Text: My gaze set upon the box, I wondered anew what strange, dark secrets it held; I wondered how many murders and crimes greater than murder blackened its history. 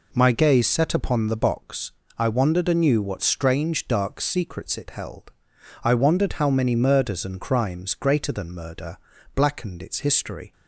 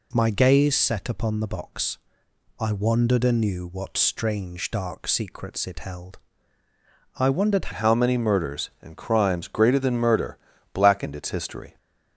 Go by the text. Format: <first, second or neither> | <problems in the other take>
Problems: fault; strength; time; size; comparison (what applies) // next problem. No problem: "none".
first | changes voice at "how"; from 7.7 s on; 4.0 s long // pauses between "murder" and "blackened"; at 10.3 s; 0.38 s long; also in the first